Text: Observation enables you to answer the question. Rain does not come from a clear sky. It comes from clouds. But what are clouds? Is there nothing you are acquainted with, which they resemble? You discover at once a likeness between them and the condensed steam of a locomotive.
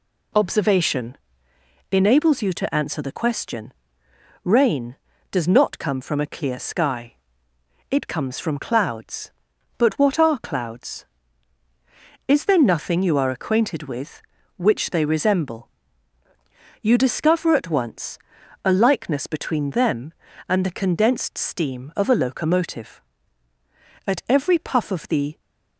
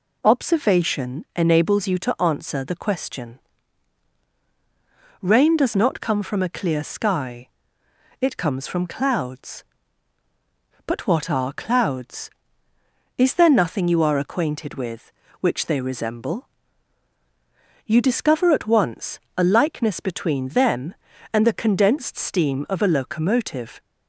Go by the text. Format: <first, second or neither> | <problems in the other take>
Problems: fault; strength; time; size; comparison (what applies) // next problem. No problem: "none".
second | pauses between "Observation" and "enables"; noticeable; at 1.1 s; 0.76 s long // pauses between "once" and "a"; at 18.1 s; 0.44 s long; slight in the second // goes on to say "At every puff of the"; from 24.0 s on; 1.3 s long